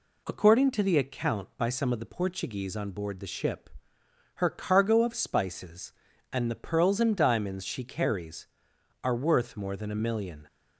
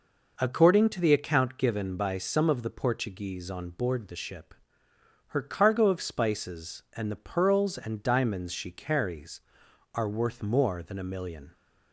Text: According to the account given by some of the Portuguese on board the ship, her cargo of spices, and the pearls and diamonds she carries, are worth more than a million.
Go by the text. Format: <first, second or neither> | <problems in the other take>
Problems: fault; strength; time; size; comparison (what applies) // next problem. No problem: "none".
second | skips "given"; at 1.5 s